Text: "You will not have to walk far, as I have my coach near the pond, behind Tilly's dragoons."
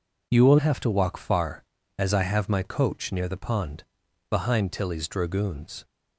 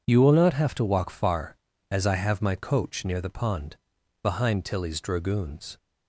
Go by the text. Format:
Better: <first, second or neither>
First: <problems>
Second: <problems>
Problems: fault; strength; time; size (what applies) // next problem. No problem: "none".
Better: second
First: skips "not"; at 0.5 s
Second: none